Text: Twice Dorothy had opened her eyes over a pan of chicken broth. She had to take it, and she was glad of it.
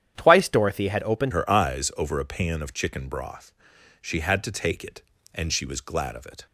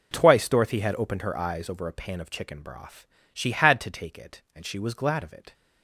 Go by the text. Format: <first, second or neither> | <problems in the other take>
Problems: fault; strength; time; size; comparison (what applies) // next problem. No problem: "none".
second | starts louder than the rest; strong; until 1.1 s; 9.5 dB // changes voice at "her"; from 1.3 s on; 5.1 s long